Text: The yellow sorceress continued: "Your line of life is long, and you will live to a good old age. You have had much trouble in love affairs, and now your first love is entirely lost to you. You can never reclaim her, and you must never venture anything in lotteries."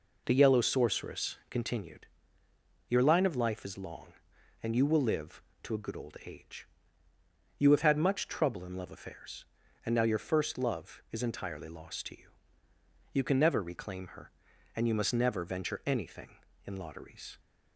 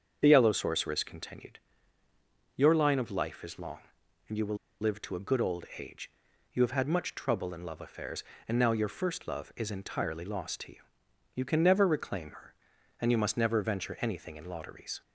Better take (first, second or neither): first